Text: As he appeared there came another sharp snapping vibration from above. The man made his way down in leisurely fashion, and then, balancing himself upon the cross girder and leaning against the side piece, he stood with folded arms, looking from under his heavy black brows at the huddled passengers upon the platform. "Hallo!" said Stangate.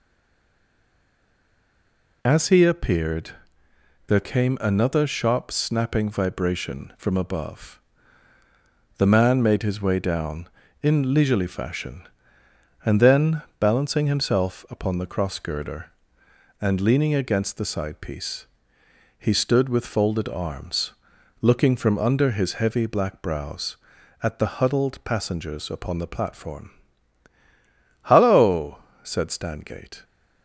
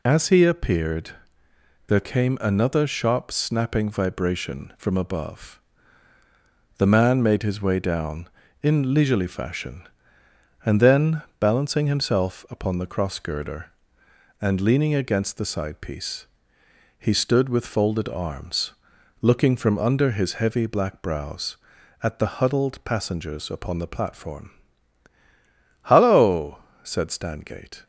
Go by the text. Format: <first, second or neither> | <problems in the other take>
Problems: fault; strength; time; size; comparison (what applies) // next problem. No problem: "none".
second | stays silent before the first word; until 2.2 s; 2.2 s long // pauses between "appeared" and "there"; noticeable; at 3.3 s; 0.74 s long; noticeable in the second